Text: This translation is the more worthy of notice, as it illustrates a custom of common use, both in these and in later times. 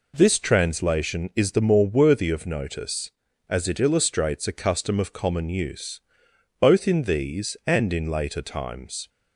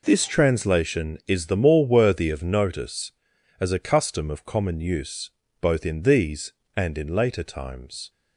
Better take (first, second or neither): first